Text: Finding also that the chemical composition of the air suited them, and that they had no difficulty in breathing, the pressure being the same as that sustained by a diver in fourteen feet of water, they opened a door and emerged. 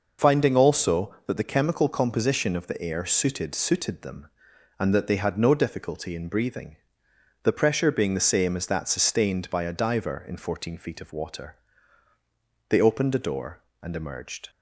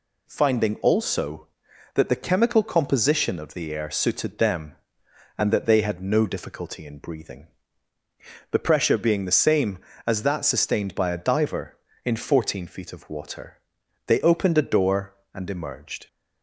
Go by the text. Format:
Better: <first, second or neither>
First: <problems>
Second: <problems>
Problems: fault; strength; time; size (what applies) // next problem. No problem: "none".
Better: second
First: says "suited" twice; at 3.5 s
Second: none